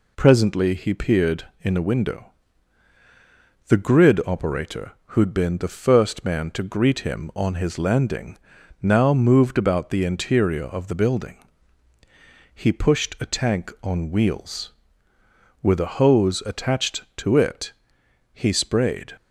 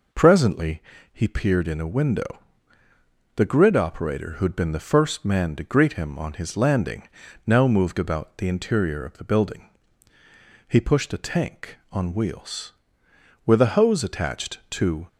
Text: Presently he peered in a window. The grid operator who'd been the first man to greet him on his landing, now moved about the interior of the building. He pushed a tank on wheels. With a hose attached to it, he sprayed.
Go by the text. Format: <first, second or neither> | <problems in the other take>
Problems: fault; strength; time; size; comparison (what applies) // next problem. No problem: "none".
first | pauses between "Presently" and "he"; slight; at 0.8 s; 0.30 s long // stops before "it he sprayed"; at 15.0 s